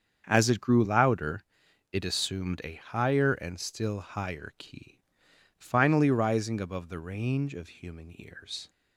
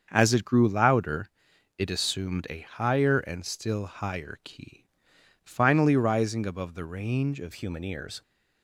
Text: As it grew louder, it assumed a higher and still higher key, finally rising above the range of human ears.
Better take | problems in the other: first | starts louder than the rest; until 1.1 s; 7 dB; strong in the first // changes voice at "human"; from 7.5 s on; 0.7 s long

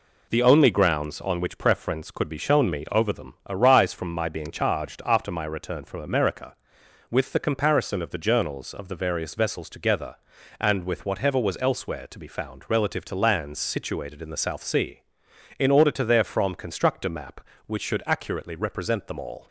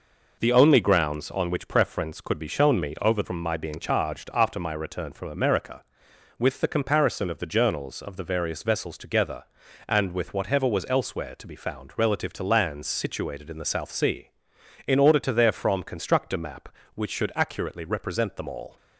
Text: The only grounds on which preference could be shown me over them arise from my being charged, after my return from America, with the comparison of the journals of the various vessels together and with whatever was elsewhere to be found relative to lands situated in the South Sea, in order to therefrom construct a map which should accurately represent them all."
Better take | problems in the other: first | skips "them arise"; at 3.2 s

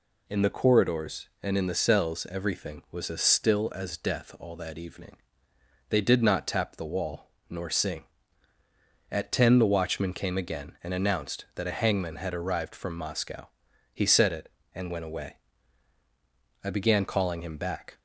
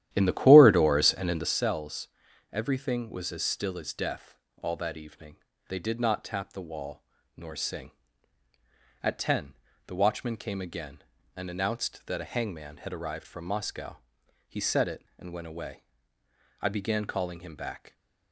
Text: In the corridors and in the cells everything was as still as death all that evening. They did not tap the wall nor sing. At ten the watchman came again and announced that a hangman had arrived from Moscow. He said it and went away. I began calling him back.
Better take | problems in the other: first | starts louder than the rest; strong; until 1.6 s; 12 dB // pauses between "cells" and "everything"; at 2.0 s; 0.42 s long // pauses between "death" and "all"; slight; at 4.3 s; 0.26 s long // pauses between "wall" and "nor"; slight; at 7.0 s; 0.36 s long; slight in the first // pauses between "ten" and "the"; slight; at 9.5 s; 0.34 s long

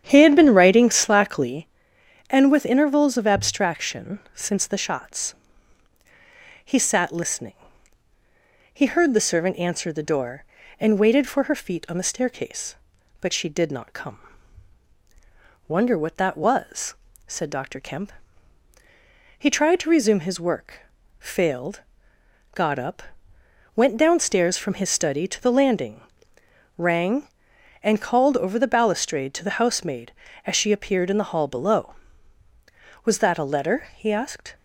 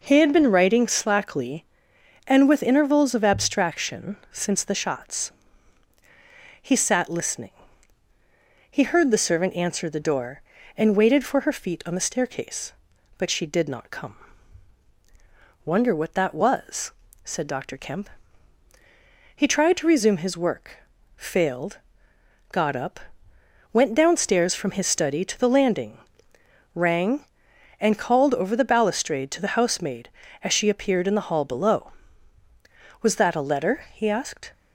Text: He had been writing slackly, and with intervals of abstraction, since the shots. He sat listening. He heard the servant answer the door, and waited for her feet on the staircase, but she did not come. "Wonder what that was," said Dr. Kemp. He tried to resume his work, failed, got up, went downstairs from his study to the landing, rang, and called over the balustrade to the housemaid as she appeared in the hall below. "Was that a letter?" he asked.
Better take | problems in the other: second | starts louder than the rest; strong; until 1.6 s; 9 dB

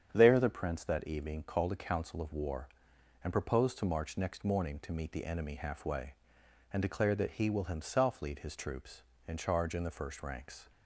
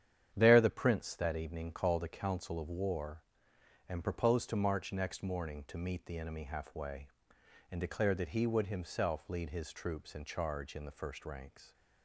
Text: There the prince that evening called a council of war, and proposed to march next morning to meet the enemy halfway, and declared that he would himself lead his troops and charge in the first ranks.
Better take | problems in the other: second | starts louder than the rest; strong; until 1.1 s; 8 dB; strong in the second // says "will" for "would"; at 7.4 s

